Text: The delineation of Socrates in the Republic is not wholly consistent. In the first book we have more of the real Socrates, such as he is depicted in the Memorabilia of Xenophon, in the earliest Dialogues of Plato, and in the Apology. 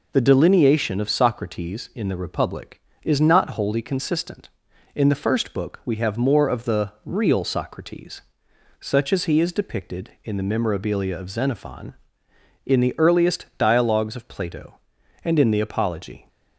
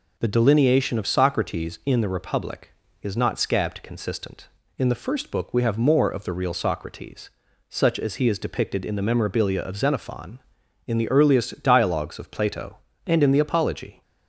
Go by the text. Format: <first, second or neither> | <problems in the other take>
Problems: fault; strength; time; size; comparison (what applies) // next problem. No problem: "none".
first | says "scabbed" for "wholly"; at 3.3 s